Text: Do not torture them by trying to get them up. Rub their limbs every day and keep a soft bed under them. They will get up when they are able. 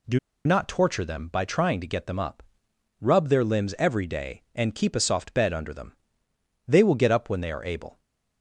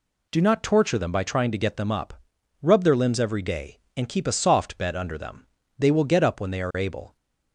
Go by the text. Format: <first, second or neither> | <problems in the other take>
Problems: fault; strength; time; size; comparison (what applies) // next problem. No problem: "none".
second | pauses between "Do" and "not"; slight; at 0.1 s; 0.27 s long